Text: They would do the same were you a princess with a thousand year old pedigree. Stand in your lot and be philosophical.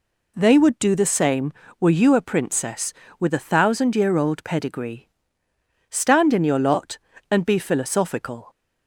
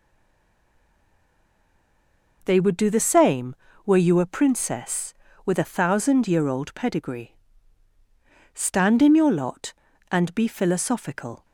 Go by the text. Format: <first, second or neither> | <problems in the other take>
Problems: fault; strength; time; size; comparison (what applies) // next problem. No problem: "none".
first | stays silent before the first word; until 2.4 s; 2.4 s long